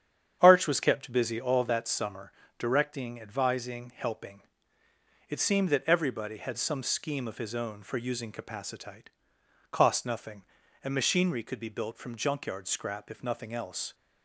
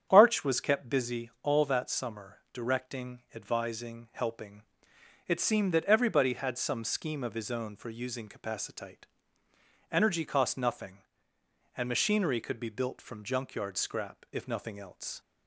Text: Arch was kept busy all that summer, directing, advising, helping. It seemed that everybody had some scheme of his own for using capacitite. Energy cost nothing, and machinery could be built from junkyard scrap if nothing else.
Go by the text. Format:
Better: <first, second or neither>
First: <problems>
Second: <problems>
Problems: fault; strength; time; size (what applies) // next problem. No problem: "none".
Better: second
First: starts louder than the rest; strong; until 1.4 s; 8.5 dB // skips "Energy"; at 9.3 s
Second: starts louder than the rest; strong; until 1.1 s; 8.5 dB